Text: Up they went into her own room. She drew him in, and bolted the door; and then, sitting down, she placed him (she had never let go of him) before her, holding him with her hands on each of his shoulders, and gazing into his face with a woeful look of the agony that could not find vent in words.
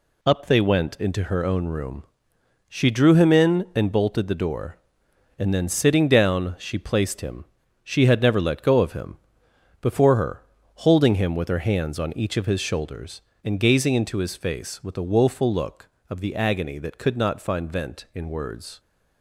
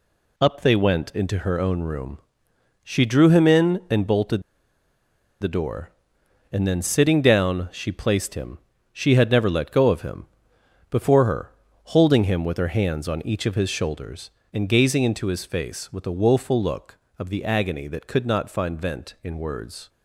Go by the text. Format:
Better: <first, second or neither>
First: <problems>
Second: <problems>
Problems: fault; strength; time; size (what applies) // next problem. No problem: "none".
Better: first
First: none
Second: pauses between "bolted" and "the"; at 4.4 s; 0.98 s long